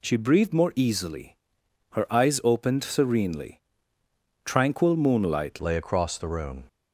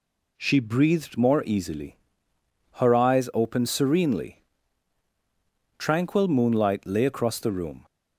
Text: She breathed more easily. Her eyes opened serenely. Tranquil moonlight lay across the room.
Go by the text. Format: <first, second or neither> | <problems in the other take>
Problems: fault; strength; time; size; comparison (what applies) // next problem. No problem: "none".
second | changes voice at "lay"; from 5.6 s on; 1.0 s long